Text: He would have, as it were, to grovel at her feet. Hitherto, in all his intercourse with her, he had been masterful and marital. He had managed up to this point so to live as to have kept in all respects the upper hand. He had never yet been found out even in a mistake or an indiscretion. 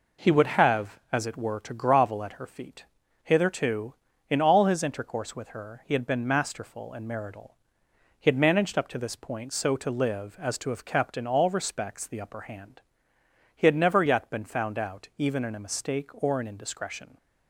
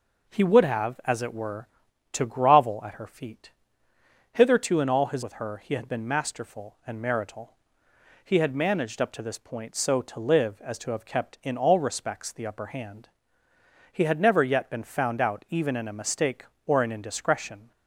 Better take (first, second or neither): first